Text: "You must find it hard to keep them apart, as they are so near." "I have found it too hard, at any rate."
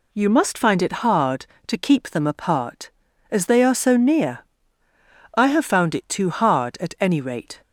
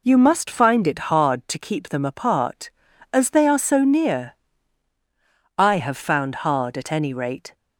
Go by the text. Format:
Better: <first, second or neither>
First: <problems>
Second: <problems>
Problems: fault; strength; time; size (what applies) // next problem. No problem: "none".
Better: first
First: none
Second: skips "it too"; at 6.4 s